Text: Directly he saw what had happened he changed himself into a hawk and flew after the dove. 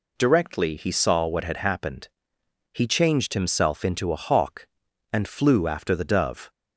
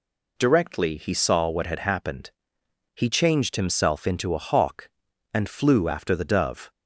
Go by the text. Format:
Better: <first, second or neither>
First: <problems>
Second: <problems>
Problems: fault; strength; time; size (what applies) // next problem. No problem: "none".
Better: neither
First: pauses between "happened" and "he"; noticeable; at 2.0 s; 0.64 s long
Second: pauses between "happened" and "he"; noticeable; at 2.3 s; 0.64 s long